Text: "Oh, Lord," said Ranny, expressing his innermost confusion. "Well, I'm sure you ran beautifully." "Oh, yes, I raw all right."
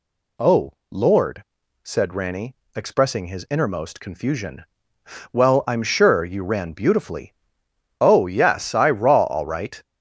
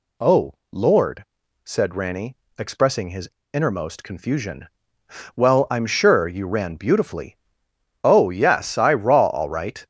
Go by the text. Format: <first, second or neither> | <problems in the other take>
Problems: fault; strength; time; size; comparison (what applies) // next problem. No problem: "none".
first | pauses between "his" and "innermost"; slight; at 3.2 s; 0.24 s long